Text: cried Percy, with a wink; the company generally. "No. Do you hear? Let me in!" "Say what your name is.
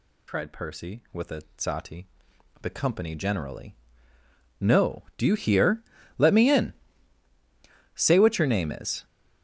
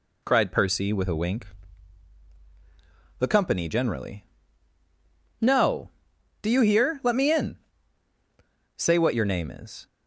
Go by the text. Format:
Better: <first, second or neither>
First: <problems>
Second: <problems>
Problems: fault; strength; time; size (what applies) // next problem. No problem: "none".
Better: second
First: says "sati" for "wink"; at 1.5 s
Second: none